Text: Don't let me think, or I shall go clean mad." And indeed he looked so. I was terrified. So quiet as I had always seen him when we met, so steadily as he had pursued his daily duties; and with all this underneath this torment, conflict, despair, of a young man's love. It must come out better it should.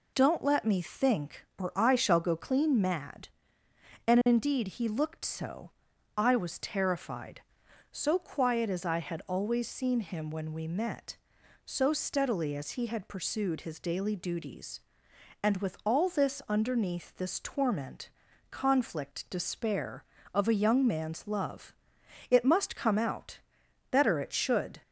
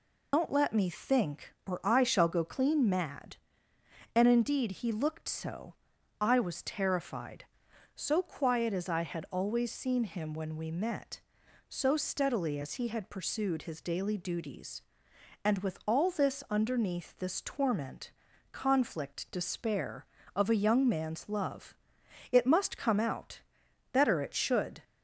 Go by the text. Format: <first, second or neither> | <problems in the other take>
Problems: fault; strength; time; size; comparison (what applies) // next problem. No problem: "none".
first | loses the start of "Don't"; at 0.3 s; 100 ms // pauses between "out" and "better"; noticeable; at 23.3 s; 0.54 s long; noticeable in the first